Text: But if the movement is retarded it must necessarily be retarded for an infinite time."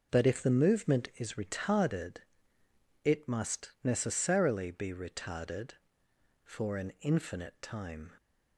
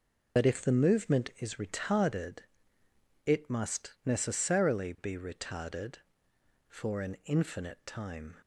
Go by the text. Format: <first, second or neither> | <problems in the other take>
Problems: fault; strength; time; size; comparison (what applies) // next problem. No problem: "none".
first | loses the start of "But"; at 0.3 s; 50 ms // pauses between "retarded" and "it"; noticeable; at 2.3 s; 0.86 s long; noticeable in the first